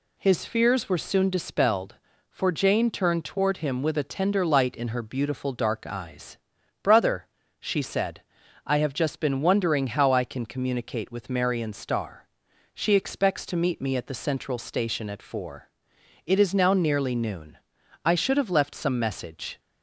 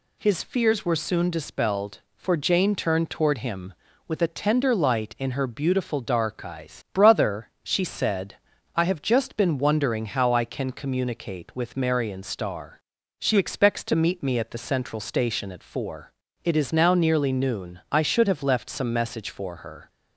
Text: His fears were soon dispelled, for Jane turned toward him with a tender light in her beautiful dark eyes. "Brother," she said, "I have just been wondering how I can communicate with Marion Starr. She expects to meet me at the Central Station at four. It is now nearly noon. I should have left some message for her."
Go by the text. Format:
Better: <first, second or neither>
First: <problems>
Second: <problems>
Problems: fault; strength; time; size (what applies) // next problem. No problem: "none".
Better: second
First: stops before "for her"; at 19.5 s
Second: none